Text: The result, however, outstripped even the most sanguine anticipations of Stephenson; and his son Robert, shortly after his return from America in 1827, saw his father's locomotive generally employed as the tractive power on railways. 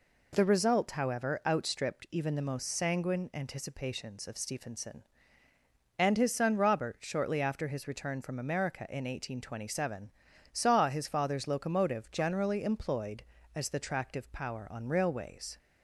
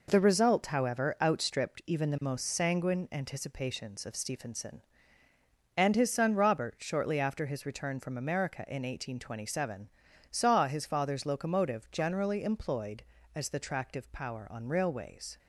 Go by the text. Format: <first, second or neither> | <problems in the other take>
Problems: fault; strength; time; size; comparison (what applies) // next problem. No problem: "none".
first | gets quieter; throughout; 6 dB